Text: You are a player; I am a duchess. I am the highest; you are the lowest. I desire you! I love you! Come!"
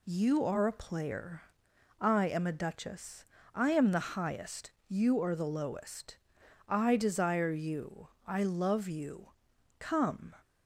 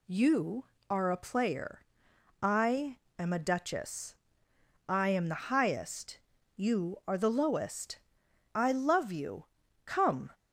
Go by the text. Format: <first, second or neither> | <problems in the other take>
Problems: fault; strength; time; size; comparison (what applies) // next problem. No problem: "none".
first | pauses between "I" and "am"; slight; at 2.9 s; 0.20 s long // skips "I desire you"; at 8.2 s